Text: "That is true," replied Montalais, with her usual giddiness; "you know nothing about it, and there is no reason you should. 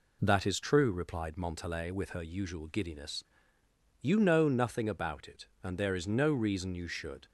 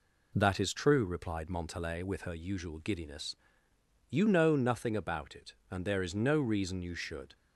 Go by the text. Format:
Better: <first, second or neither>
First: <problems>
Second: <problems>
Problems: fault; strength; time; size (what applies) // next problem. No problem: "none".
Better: neither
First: none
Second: none